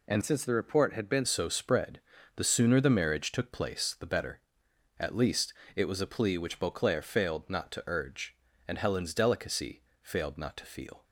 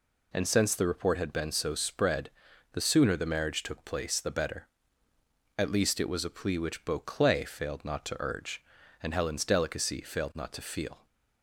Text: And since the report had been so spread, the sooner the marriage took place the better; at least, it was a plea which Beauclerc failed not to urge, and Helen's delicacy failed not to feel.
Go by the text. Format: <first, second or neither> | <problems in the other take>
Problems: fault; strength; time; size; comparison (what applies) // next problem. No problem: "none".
second | changes voice from "since" to "been"; from 0.2 to 1.2 s; 1.0 s long // pauses between "delicacy" and "failed"; slight; at 9.8 s; 0.18 s long